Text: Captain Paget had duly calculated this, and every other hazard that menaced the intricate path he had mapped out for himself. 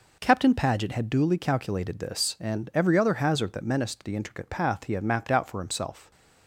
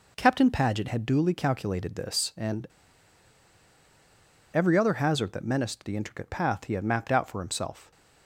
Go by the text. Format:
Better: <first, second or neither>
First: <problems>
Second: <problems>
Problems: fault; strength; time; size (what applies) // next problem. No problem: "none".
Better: first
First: none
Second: pauses between "and" and "every"; strong; at 2.6 s; 1.8 s long